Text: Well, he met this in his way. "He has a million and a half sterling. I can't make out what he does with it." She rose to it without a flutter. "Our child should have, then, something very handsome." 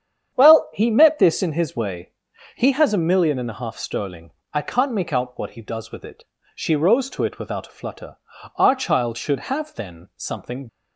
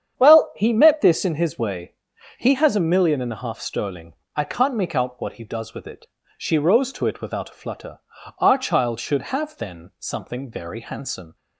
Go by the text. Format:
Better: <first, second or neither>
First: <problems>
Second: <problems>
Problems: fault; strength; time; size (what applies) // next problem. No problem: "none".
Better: second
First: starts louder than the rest; strong; until 1.3 s; 8.5 dB // stops before "very handsome"; at 10.6 s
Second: starts louder than the rest; strong; until 1.2 s; 8.5 dB